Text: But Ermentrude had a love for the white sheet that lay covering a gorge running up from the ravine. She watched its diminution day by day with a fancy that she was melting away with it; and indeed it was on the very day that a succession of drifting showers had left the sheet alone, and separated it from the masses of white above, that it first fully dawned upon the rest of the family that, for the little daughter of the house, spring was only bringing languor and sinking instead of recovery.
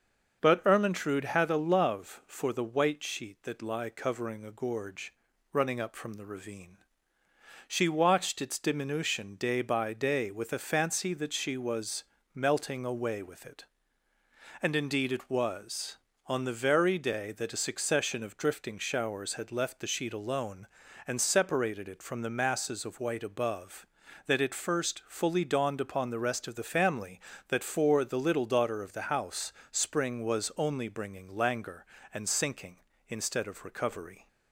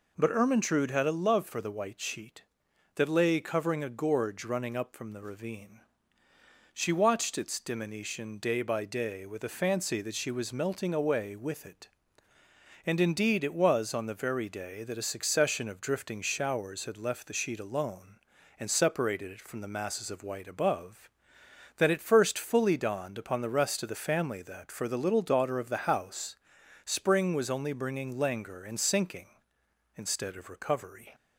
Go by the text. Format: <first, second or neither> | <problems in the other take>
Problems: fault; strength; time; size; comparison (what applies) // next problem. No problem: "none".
second | starts louder than the rest; until 1.4 s; 6.5 dB // says "lie" for "lay"; at 3.6 s // pauses between "gorge" and "running"; at 5.1 s; 0.38 s long // pauses between "was" and "melting"; slight; at 12.0 s; 0.30 s long